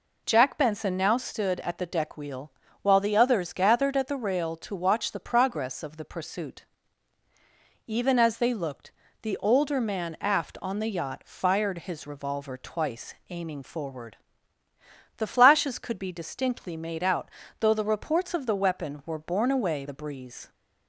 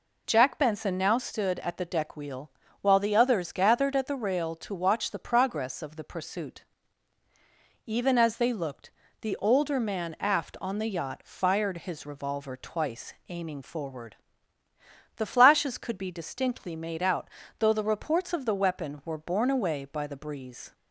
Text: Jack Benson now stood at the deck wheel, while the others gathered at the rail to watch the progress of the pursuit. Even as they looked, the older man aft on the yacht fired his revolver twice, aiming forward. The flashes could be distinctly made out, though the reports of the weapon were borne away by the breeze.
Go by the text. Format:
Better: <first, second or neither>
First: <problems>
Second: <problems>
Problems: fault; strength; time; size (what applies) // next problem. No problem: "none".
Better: second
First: skips "by"; at 19.8 s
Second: none